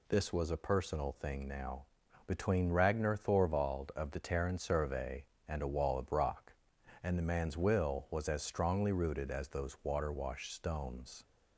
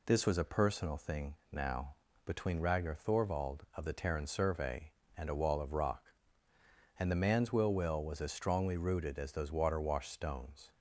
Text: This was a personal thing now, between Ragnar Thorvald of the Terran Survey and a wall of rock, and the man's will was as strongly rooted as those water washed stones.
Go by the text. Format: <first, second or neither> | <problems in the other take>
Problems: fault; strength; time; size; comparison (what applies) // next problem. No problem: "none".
first | pauses between "thing" and "now"; slight; at 1.3 s; 0.16 s long // says "will" twice; at 7.7 s